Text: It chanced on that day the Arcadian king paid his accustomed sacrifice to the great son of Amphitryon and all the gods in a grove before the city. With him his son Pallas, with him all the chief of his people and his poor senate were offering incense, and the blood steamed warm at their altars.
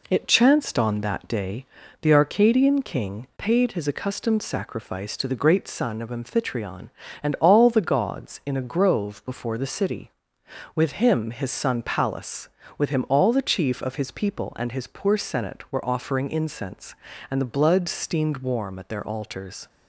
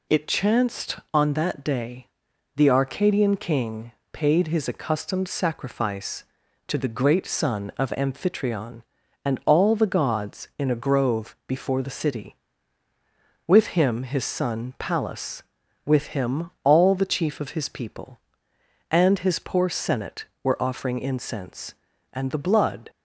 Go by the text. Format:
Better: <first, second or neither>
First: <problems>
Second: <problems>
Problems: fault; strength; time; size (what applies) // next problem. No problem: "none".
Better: first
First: pauses between "day" and "the"; at 1.6 s; 0.38 s long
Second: pauses between "day" and "the"; noticeable; at 2.0 s; 0.50 s long // pauses between "king" and "paid"; slight; at 3.9 s; 0.20 s long // stops before "steamed warm at their altars"; at 22.8 s